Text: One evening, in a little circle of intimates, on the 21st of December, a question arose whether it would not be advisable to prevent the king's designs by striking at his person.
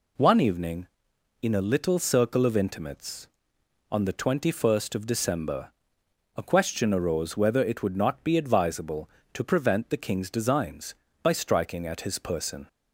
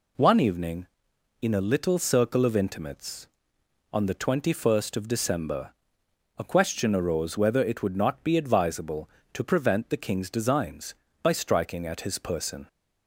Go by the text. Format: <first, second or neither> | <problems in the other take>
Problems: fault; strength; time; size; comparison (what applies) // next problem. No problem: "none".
neither | none